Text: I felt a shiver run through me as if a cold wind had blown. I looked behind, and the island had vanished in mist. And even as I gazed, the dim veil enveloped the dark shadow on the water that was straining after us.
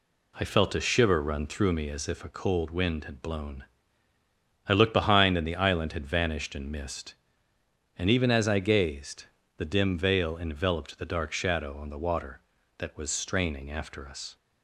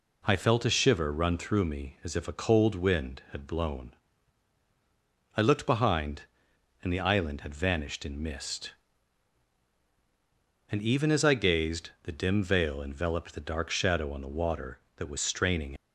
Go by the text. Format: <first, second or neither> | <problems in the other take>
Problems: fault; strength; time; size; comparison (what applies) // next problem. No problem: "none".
first | stops before "after us"; at 15.7 s